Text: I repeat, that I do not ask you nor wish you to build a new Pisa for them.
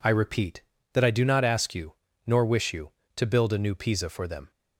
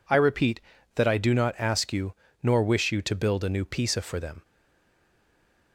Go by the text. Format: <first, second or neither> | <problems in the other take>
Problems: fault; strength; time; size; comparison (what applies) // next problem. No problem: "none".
first | pauses between "you" and "nor"; slight; at 2.1 s; 0.28 s long; slight in the first // stays silent after the last word; noticeable; from 4.4 s on; 1.3 s long